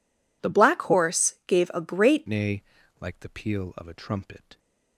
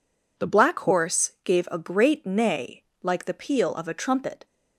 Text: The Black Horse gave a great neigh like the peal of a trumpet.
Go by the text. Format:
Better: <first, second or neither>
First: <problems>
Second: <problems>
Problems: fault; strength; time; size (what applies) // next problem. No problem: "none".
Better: second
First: changes voice at "neigh"; from 2.2 s on; 2.3 s long // pauses between "neigh" and "like"; at 2.6 s; 0.38 s long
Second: pauses between "neigh" and "like"; slight; at 2.8 s; 0.18 s long